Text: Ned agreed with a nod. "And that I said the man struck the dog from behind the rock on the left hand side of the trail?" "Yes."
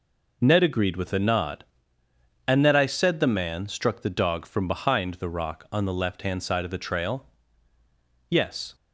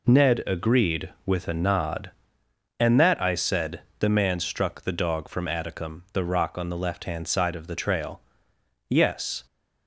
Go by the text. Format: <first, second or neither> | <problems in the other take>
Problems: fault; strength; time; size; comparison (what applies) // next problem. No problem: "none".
first | pauses between "said" and "the"; slight; at 3.8 s; 0.16 s long // says "atticum" for "behind"; at 5.4 s